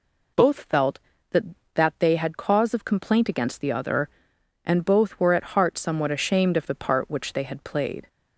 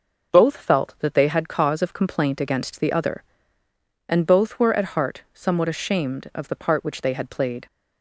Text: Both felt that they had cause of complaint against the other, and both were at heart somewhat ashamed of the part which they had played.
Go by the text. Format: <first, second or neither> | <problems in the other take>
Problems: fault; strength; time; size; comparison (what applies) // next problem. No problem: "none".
second | says "that" twice; at 1.7 s